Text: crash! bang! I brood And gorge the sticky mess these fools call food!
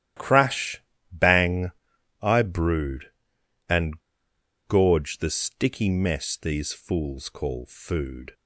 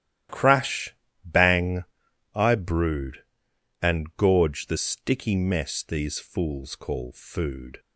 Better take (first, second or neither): second